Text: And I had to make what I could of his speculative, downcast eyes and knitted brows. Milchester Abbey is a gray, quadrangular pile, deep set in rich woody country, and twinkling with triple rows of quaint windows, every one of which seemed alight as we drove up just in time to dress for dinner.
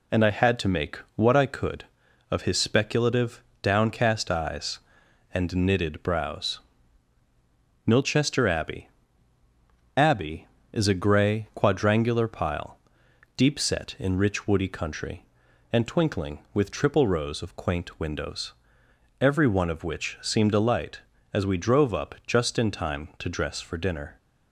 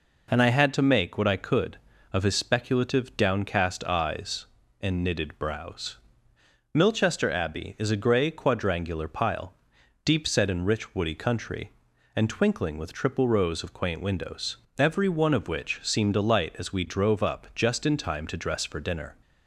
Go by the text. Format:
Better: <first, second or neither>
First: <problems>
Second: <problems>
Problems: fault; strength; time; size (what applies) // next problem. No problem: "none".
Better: second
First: pauses between "make" and "what"; slight; at 0.9 s; 0.16 s long // says "Abbey" twice; at 9.9 s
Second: none